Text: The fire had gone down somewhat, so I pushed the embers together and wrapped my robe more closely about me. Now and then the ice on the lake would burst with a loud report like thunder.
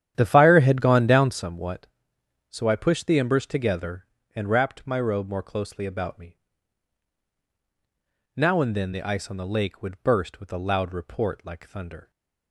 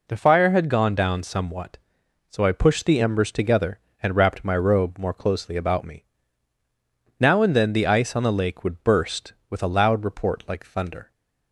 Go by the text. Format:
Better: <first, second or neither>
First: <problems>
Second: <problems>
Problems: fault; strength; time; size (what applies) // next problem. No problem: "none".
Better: second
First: starts louder than the rest; strong; until 1.4 s; 10.5 dB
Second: none